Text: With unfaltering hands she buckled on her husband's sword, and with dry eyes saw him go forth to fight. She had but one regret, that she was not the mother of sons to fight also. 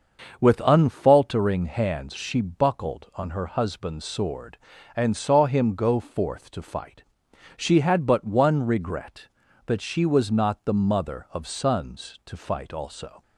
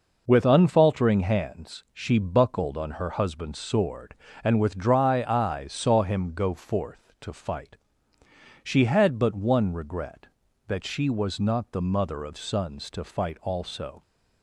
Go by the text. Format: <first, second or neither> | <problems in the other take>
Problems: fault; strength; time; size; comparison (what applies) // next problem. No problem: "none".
second | starts louder than the rest; until 1.4 s; 6.5 dB // skips "with dry eyes"; at 5.1 s